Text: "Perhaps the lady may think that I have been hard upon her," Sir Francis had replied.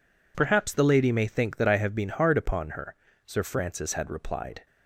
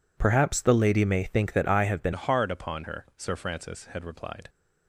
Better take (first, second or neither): first